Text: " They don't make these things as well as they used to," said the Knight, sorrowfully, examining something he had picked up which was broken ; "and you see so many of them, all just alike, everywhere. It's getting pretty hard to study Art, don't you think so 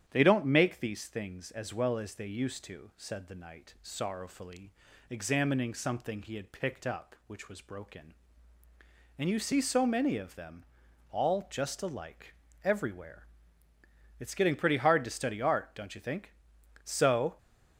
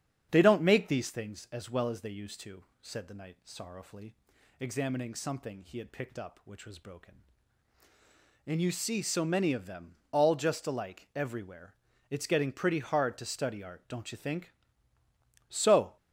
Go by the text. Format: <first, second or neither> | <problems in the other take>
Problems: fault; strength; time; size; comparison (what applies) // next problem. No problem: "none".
neither | starts louder than the rest; strong; the same in both